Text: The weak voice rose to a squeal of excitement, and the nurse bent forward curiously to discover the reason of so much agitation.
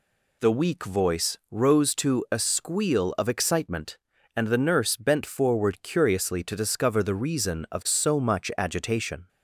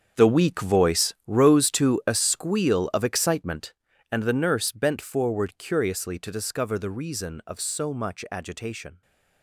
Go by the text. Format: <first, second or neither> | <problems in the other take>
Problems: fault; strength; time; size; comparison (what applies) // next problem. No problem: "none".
first | gets quieter; strong; throughout; 15 dB